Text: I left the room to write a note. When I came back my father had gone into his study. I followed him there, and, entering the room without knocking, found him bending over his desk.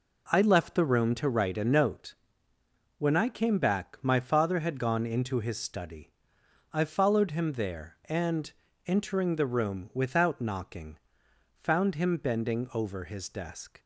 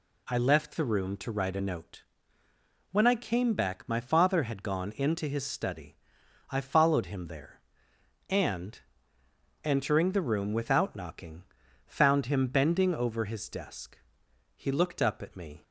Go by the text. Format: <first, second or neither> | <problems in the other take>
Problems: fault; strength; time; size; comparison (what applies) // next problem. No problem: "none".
first | goes on to say "He looked up at me"; noticeable; from 14.5 s on; 1.0 s long